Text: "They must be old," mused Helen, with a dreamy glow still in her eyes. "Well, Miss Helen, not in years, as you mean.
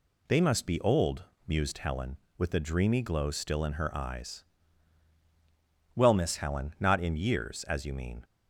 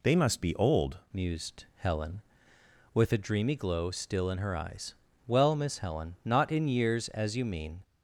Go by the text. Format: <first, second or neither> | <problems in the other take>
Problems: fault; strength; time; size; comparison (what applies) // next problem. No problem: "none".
first | changes voice at "mused"; from 1.1 s on; 6.7 s long